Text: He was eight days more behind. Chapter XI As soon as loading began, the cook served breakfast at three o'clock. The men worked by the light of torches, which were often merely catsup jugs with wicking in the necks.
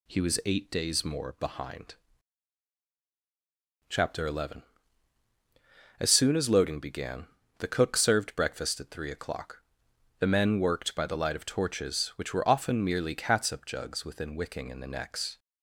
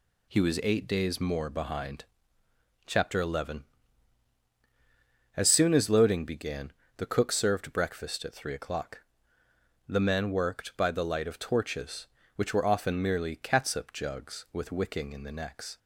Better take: second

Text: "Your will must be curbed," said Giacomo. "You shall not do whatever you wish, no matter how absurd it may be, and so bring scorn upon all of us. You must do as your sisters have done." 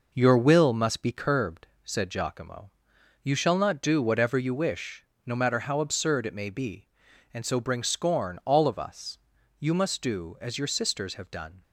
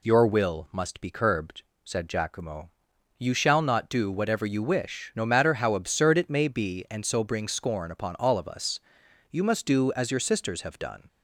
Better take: second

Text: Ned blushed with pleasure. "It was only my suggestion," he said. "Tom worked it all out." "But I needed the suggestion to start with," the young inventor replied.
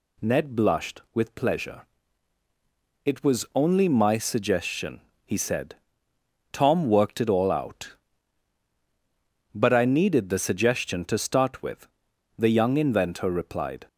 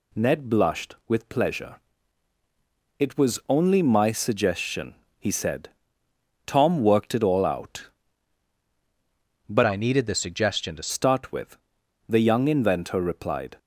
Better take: first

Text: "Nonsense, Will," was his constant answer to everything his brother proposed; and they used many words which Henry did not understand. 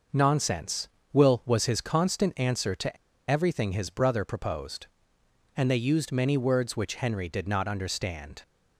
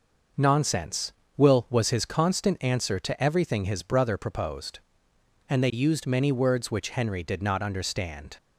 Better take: second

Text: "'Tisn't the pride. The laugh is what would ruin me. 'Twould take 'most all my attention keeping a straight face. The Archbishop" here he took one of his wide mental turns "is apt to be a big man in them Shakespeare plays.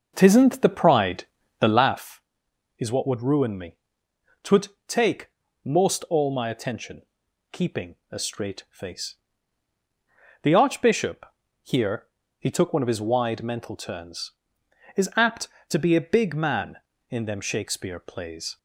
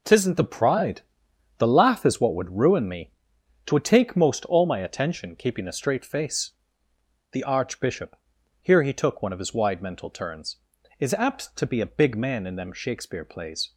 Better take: second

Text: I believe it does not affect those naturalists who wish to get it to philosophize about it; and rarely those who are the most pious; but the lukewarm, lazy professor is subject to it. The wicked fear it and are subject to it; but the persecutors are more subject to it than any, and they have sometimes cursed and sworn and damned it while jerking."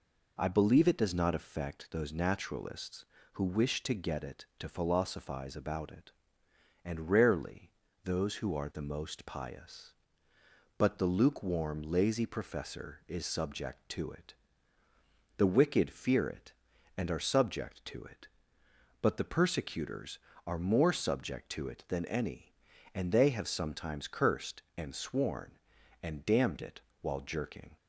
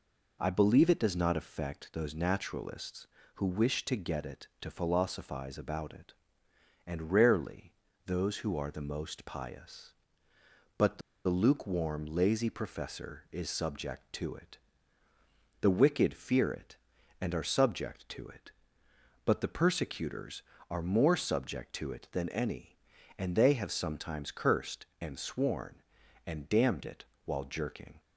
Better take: first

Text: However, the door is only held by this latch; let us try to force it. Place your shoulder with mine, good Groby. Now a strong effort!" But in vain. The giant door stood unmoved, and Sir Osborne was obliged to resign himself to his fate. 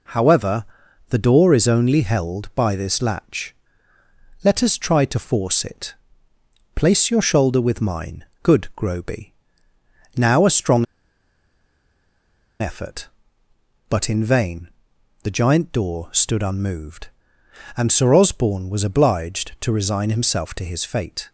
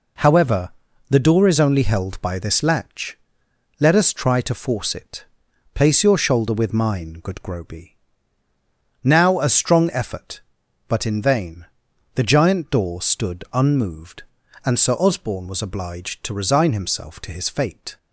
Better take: second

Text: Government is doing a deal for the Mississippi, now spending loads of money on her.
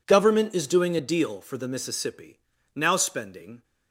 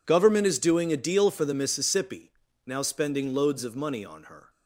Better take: second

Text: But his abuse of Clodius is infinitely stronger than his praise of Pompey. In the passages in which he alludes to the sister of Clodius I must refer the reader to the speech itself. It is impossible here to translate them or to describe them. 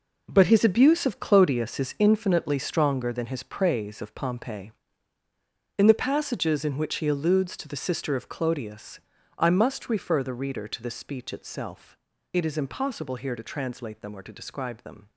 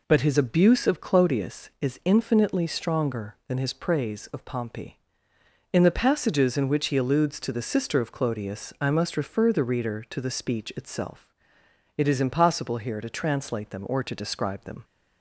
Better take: second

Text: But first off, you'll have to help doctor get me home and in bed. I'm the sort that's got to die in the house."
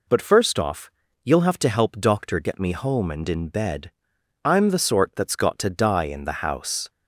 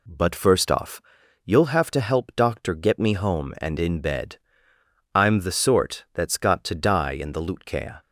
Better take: first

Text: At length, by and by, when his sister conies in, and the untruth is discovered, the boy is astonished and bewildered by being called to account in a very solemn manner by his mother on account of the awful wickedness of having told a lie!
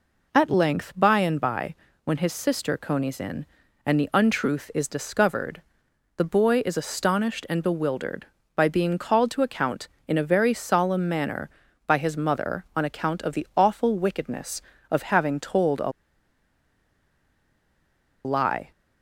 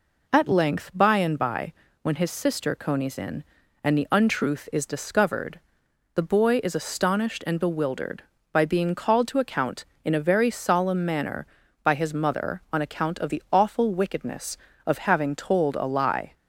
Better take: second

